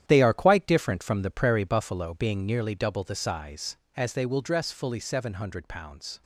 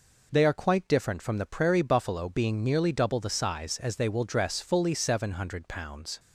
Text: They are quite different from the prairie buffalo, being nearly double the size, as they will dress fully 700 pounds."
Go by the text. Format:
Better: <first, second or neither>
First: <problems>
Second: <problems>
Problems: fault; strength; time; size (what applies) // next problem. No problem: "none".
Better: second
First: gets quieter; strong; throughout; 10.5 dB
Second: none